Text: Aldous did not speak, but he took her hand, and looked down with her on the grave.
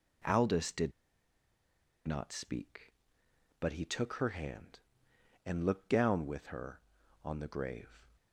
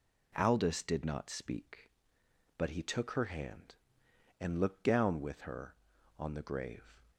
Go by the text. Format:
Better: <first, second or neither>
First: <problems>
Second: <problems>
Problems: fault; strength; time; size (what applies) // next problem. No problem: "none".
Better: second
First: pauses between "did" and "not"; at 0.9 s; 1.1 s long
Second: none